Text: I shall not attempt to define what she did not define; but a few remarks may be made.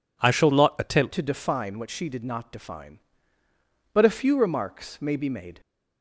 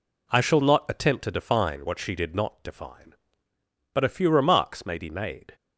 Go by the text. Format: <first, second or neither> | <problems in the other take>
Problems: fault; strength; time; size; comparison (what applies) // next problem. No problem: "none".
second | changes voice at "to"; from 1.1 s on; 4.5 s long